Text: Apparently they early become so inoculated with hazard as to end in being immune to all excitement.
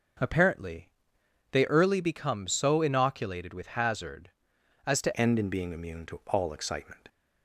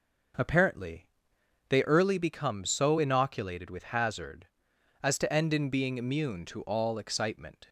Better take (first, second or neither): second